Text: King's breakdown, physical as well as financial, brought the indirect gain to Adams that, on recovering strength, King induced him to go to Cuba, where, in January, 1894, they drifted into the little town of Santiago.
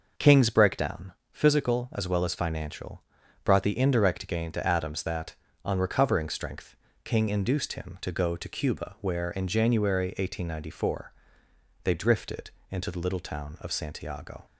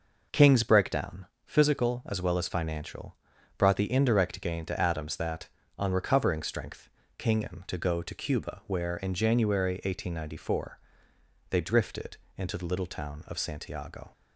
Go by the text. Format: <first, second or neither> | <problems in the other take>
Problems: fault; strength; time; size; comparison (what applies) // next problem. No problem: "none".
first | skips "induced"; at 7.4 s // pauses between "drifted" and "into"; slight; at 12.1 s; 0.22 s long; slight in the first